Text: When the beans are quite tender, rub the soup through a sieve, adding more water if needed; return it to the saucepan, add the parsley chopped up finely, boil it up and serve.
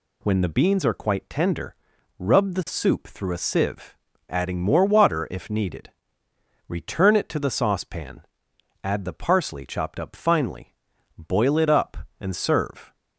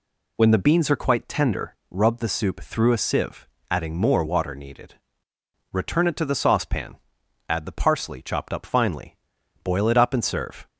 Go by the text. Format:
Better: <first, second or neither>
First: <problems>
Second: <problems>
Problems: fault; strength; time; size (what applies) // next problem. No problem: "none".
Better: first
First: none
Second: skips "if"; at 4.5 s